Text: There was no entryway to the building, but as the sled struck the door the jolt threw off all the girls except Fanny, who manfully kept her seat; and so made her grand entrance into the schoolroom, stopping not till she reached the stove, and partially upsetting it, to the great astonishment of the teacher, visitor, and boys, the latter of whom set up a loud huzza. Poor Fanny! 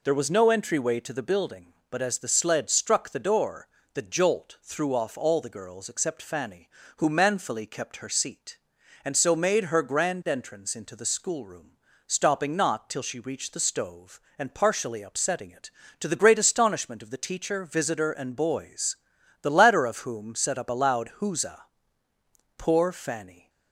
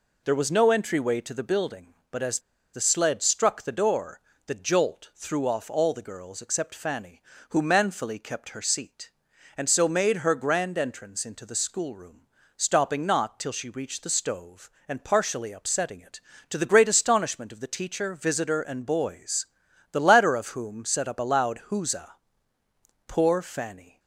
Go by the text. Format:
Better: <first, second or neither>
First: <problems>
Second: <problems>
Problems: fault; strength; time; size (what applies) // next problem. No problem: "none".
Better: first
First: pauses between "door" and "the"; slight; at 3.6 s; 0.26 s long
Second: pauses between "as" and "the"; slight; at 2.3 s; 0.34 s long // pauses between "door" and "the"; slight; at 4.2 s; 0.26 s long